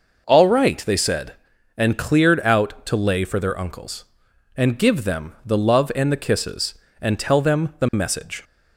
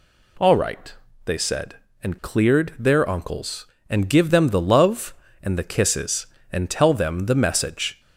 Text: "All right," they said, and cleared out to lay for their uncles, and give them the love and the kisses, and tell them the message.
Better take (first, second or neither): first